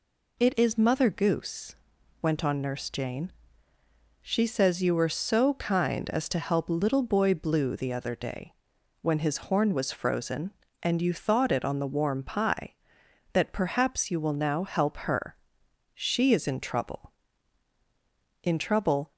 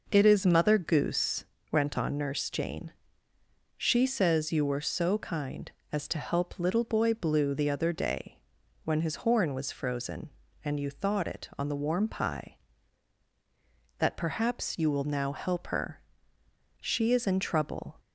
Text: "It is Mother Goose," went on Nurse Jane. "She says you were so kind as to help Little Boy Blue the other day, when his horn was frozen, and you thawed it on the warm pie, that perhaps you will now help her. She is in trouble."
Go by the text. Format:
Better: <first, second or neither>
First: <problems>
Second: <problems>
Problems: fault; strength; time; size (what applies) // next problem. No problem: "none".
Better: second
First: goes on to say "In trouble"; noticeable; from 18.4 s on; 0.70 s long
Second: none